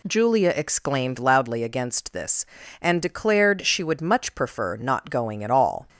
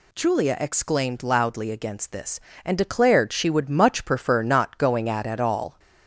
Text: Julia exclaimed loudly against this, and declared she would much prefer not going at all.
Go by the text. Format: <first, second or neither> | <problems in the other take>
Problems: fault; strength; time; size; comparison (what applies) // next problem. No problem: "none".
first | says "at" twice; at 5.2 s